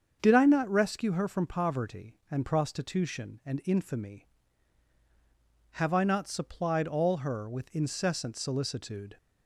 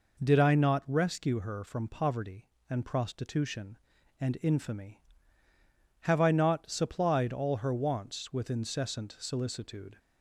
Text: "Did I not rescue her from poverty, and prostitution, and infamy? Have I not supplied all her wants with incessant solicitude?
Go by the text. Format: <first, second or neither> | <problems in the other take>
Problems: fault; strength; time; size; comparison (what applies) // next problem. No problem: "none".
second | starts louder than the rest; strong; until 1.2 s; 7 dB // skips "wants"; at 7.4 s